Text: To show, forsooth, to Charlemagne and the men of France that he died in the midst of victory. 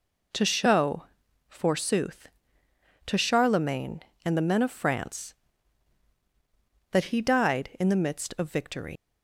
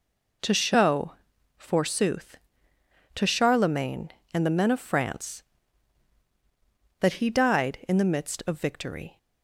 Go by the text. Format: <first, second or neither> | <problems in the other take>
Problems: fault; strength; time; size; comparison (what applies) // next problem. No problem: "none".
second | leaves "victory" unfinished; at 8.9 s; 130 ms